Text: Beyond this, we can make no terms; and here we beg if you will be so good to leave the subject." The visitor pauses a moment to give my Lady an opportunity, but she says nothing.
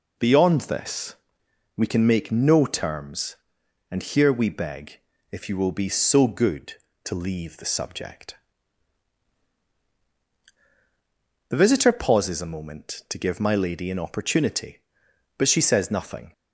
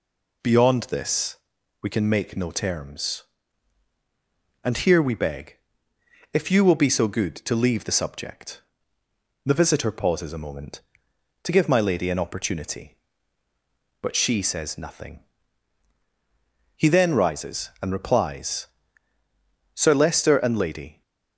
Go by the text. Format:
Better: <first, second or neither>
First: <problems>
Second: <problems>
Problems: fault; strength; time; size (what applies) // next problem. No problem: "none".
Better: first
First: pauses between "beg" and "if"; slight; at 4.9 s; 0.32 s long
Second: pauses between "beg" and "if"; noticeable; at 5.5 s; 0.74 s long // goes on to say "He then rises and replies Sir Leicester and Lady"; strong; from 16.7 s on; 4.2 s long